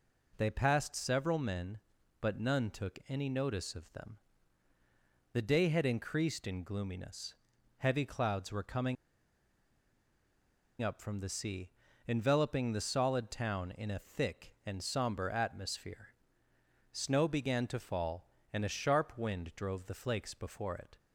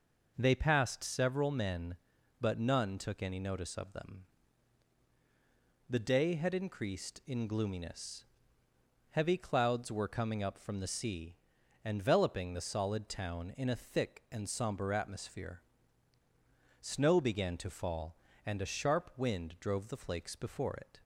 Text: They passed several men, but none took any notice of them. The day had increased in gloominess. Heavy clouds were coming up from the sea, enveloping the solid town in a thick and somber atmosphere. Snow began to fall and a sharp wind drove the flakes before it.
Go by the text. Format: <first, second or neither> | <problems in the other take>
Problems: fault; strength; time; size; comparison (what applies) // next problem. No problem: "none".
second | pauses between "coming" and "up"; strong; at 8.9 s; 1.8 s long